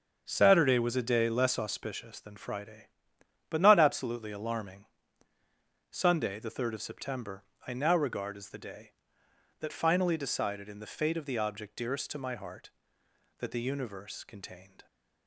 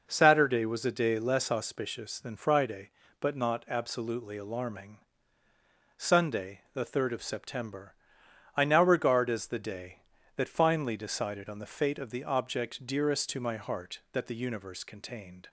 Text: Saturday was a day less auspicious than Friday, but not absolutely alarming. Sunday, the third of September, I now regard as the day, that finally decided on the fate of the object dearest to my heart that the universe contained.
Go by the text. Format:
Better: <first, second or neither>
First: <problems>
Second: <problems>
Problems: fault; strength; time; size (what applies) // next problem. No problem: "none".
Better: second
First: starts louder than the rest; strong; until 1.2 s; 7 dB // says "in" for "on"; at 10.6 s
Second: none